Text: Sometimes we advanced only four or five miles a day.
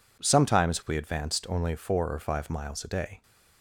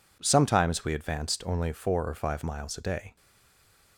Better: first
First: none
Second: stays silent after the last word; slight; from 3.1 s on; 0.8 s long

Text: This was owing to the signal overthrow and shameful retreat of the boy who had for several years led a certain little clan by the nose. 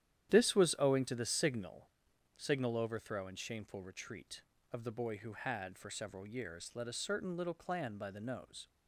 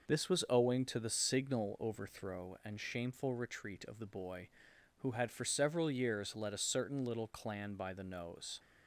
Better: second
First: starts louder than the rest; strong; until 1.3 s; 11 dB // says "signal" twice; at 2.3 s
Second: none

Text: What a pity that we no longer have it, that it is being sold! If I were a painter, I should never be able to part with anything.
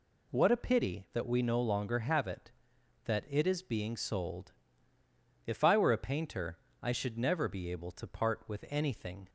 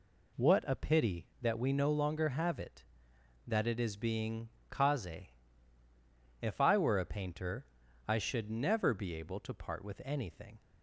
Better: first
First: none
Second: says "kaze" for "sold"; at 4.7 s

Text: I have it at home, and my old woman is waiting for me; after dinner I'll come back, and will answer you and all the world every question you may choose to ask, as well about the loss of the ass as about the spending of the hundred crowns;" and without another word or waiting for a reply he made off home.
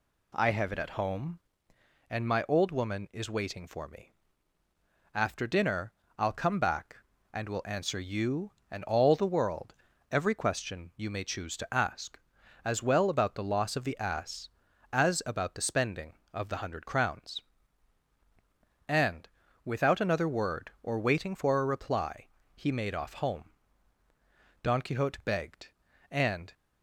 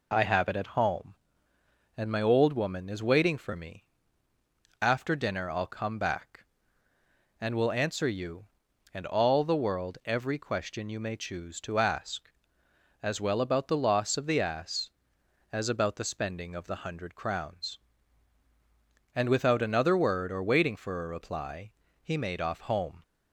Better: second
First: pauses between "dinner" and "I'll"; slight; at 5.9 s; 0.26 s long // pauses between "world" and "every"; slight; at 9.7 s; 0.34 s long // pauses between "and" and "without"; slight; at 19.2 s; 0.36 s long // pauses between "reply" and "he"; slight; at 22.2 s; 0.30 s long // goes on to say "Don Quixote begged and"; strong; from 24.6 s on; 1.9 s long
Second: pauses between "reply" and "he"; slight; at 21.7 s; 0.30 s long

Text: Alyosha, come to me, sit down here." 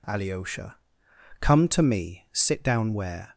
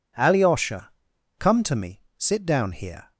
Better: second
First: says "where" for "here"; at 2.9 s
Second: none

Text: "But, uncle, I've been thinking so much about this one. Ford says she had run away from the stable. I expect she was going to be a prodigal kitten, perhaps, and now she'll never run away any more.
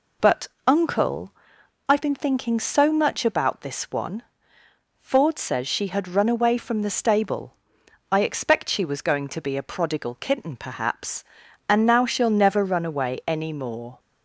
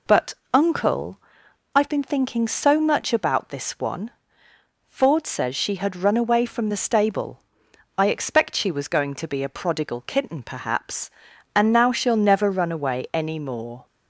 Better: neither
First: none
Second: none

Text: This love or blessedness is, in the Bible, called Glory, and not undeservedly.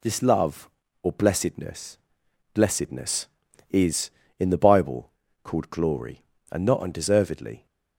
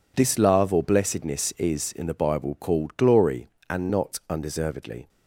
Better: second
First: says "blessedness" twice; at 2.5 s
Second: none

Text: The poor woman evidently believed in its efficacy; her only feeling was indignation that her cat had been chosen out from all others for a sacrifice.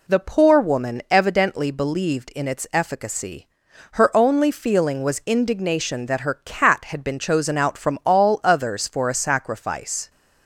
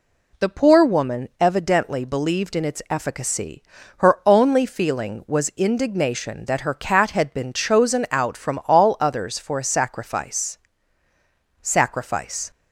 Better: first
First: none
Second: says "sacrifice" twice; at 11.6 s

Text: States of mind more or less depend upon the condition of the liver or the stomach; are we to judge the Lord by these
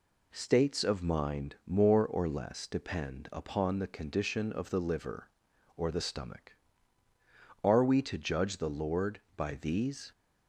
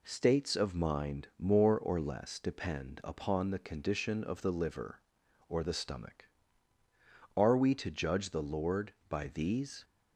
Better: neither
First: none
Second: none

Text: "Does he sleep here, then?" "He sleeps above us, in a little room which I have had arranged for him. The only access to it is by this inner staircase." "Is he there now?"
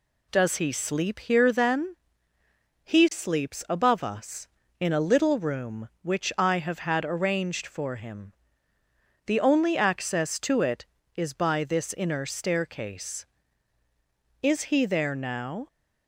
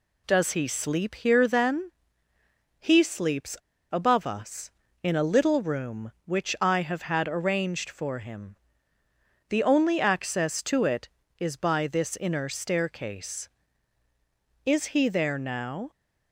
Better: first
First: none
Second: pauses between "sleeps" and "above"; slight; at 3.5 s; 0.34 s long

